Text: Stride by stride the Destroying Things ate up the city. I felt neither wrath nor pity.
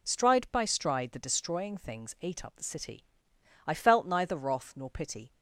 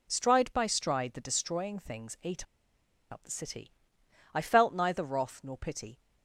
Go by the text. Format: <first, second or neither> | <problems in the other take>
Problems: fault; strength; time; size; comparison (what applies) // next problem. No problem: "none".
first | pauses between "ate" and "up"; noticeable; at 2.4 s; 0.66 s long